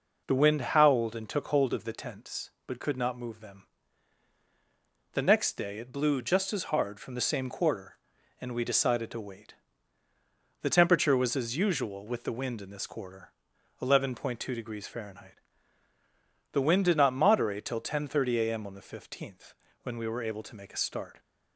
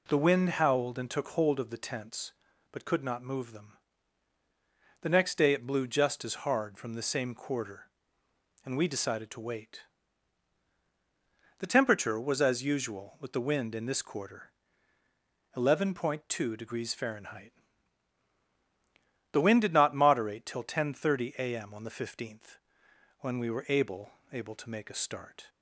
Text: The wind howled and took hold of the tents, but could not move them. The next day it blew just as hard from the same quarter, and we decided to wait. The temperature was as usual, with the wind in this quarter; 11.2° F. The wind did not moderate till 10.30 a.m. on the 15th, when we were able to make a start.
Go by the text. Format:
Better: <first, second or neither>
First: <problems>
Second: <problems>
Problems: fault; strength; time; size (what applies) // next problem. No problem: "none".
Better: first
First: none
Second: says "able" twice; at 24.3 s